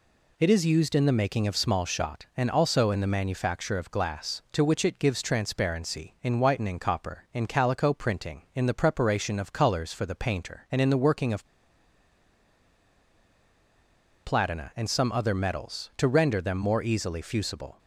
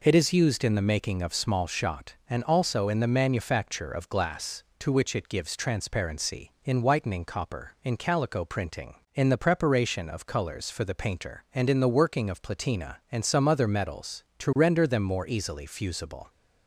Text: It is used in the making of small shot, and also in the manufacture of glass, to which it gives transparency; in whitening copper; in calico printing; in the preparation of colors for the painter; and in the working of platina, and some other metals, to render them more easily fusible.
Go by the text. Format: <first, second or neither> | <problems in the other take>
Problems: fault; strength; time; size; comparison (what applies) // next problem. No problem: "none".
second | pauses between "of" and "platina"; strong; at 11.4 s; 2.7 s long